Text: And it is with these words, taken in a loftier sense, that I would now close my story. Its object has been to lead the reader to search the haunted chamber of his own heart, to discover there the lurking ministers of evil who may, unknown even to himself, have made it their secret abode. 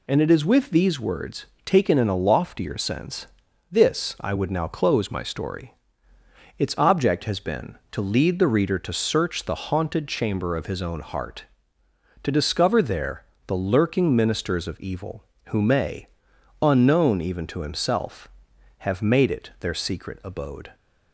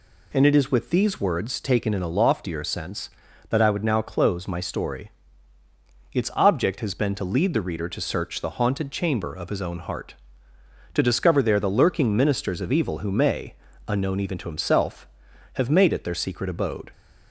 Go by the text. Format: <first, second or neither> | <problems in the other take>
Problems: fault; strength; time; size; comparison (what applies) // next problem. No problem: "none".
second | says "this" for "that"; at 3.7 s // pauses between "there" and "the"; slight; at 13.2 s; 0.22 s long